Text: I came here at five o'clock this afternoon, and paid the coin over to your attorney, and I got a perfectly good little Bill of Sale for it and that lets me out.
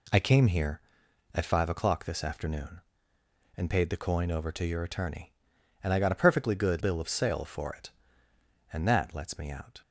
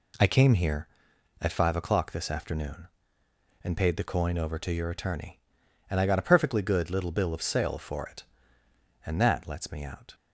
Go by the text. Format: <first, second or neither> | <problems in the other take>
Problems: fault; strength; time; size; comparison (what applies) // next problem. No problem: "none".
second | skips "little"; at 6.8 s